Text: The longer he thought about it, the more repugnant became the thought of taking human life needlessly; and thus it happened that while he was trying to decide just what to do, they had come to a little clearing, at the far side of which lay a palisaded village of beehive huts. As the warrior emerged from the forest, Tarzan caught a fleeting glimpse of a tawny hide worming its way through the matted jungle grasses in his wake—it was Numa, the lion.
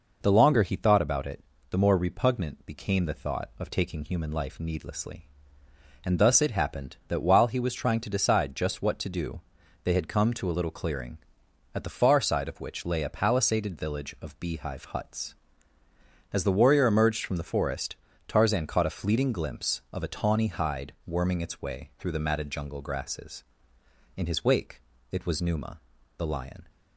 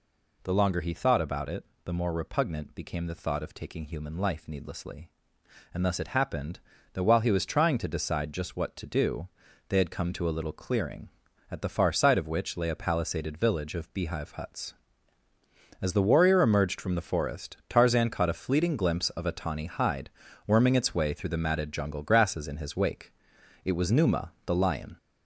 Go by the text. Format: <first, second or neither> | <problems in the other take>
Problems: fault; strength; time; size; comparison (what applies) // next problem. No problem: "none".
first | gets louder; noticeable; throughout; 5 dB // pauses between "hide" and "worming"; at 20.0 s; 0.38 s long